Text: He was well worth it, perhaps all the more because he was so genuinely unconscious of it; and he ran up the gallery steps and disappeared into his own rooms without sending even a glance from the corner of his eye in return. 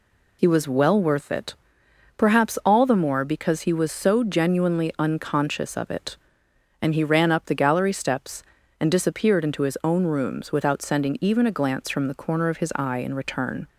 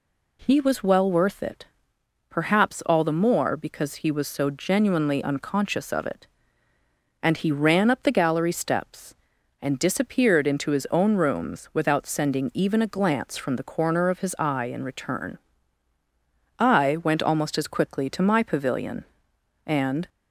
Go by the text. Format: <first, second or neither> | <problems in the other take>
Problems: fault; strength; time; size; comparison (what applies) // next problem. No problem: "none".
first | goes on to say "I went almost as quickly to my pavilion and"; strong; from 16.5 s on; 3.5 s long